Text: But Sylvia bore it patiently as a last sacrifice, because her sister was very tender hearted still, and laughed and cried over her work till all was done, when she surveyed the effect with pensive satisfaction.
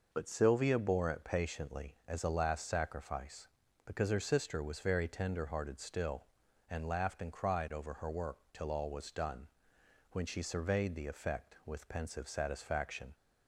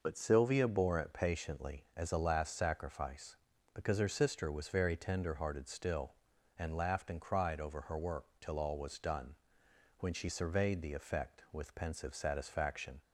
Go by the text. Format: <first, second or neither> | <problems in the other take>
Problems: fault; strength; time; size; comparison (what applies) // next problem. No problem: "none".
neither | none